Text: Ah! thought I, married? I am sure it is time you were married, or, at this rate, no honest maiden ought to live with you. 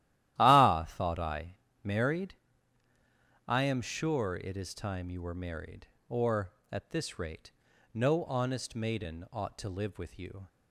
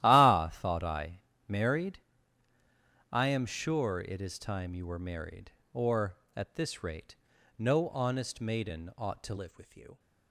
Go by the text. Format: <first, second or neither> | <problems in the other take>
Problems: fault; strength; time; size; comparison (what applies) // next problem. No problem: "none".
first | starts louder than the rest; strong; until 1.0 s; 13.5 dB; strong in the first // changes voice at "live"; from 9.3 s on; 0.6 s long